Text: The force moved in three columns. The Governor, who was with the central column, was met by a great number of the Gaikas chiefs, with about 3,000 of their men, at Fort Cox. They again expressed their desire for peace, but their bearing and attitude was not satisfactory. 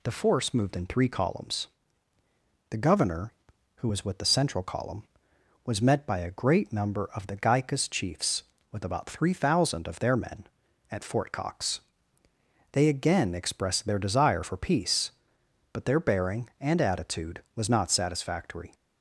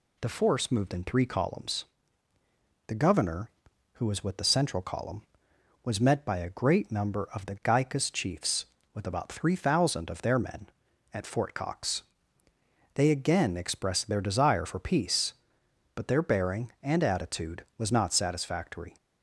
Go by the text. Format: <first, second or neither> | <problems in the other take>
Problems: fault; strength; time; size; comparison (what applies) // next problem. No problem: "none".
neither | none